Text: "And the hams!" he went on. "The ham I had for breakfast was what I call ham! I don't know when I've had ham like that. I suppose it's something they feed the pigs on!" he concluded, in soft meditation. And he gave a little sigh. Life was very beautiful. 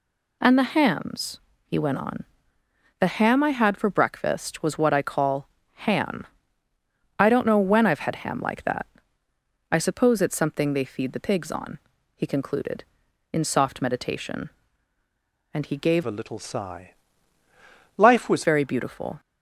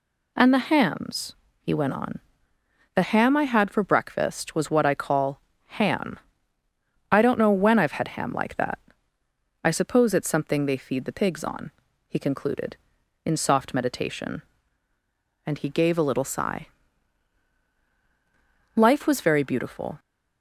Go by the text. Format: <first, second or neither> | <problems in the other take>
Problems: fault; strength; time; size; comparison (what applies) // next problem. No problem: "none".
second | pauses between "call" and "ham"; slight; at 5.4 s; 0.24 s long; slight in the second // changes voice from "a" to "was"; from 16.0 to 18.4 s; 2.4 s long